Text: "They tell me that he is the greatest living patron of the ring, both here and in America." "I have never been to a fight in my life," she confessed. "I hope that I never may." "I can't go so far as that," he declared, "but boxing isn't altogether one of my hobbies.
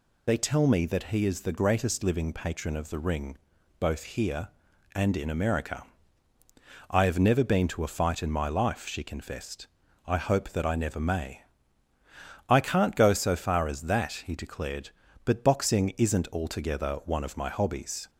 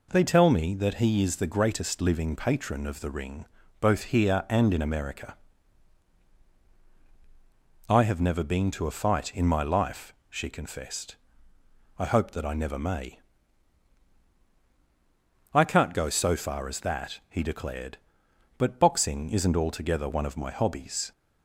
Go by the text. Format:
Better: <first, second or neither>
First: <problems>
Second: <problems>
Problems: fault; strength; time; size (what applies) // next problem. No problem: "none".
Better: second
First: loses the start of "They"; at 0.2 s; 40 ms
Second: none